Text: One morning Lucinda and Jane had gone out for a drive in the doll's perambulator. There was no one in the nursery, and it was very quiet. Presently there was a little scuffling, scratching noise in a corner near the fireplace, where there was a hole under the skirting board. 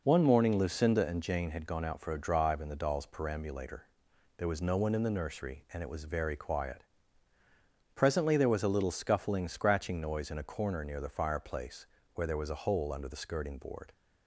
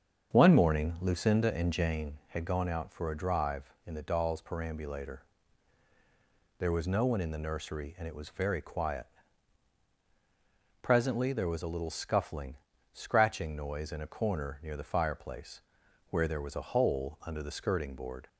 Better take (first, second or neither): first